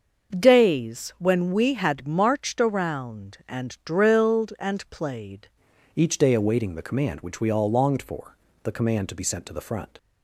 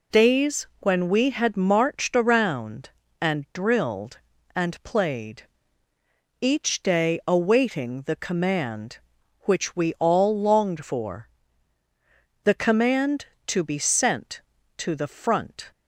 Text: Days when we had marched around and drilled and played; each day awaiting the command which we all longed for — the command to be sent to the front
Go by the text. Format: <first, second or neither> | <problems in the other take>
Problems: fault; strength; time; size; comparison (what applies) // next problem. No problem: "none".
second | starts louder than the rest; until 1.4 s; 6.5 dB // changes voice at "each"; from 5.9 s on; 4.0 s long